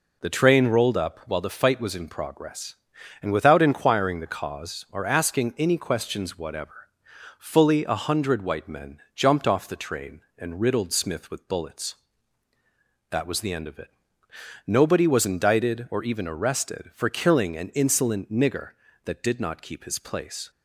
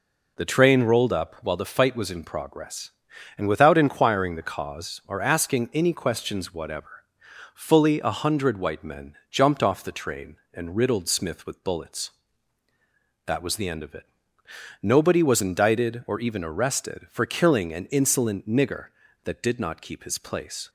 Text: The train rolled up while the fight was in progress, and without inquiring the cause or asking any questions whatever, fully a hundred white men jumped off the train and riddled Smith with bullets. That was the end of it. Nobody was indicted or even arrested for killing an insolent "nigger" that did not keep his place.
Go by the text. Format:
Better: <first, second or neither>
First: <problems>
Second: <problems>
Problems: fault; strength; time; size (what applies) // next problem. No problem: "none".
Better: neither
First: pauses between "men" and "jumped"; slight; at 8.9 s; 0.16 s long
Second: pauses between "men" and "jumped"; slight; at 9.1 s; 0.16 s long